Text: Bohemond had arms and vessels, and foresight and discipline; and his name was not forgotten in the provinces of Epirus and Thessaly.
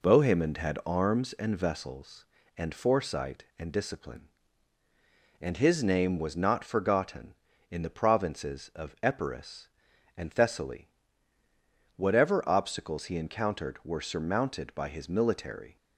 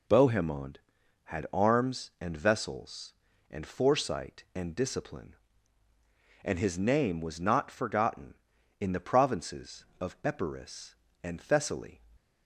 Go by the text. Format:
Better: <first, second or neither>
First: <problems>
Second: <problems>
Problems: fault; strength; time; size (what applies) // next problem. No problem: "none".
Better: second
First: goes on to say "Whatever obstacles he encountered were surmounted by his military"; strong; from 11.9 s on; 3.8 s long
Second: none